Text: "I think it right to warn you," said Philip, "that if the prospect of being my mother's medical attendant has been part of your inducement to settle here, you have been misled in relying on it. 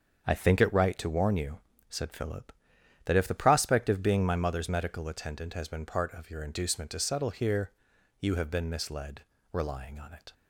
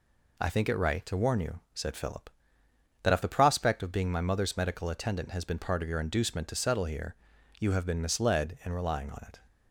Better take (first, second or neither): second